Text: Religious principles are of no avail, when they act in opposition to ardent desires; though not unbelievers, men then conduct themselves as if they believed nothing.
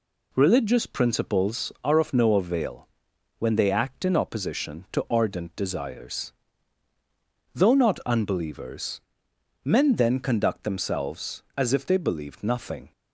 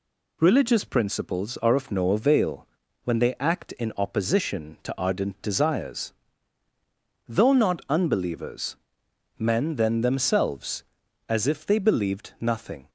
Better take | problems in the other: first | skips "conduct"; at 10.0 s

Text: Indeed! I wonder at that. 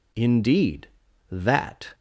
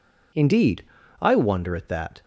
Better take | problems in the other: second | skips "I wonder at"; at 1.0 s

